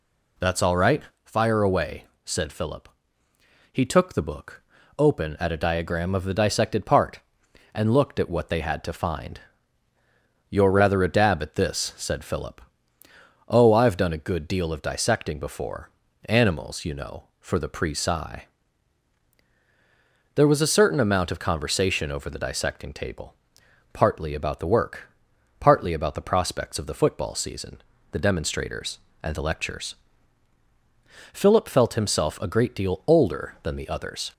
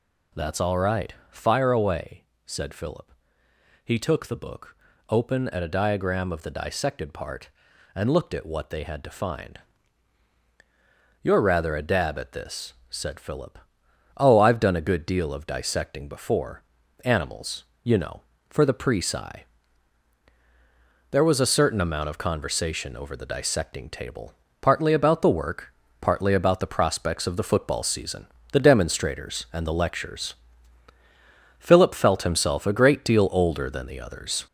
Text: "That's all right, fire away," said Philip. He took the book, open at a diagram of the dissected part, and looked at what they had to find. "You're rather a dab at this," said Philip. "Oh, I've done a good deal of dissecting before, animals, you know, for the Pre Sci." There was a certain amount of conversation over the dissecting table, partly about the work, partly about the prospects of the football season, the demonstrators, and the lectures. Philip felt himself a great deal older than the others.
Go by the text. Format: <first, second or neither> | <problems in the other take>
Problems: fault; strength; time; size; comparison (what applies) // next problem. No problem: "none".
first | gets louder; noticeable; throughout; 5 dB